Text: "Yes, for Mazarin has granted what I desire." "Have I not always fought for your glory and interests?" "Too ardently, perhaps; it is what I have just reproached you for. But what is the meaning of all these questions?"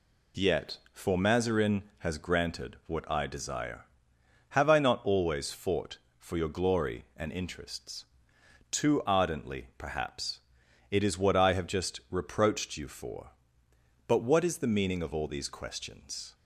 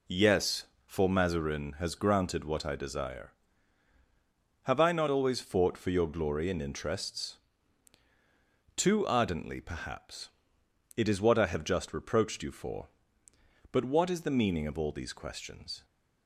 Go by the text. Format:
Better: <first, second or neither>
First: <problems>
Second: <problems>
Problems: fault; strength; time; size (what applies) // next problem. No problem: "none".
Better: second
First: says "Yet" for "Yes"; at 0.3 s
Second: none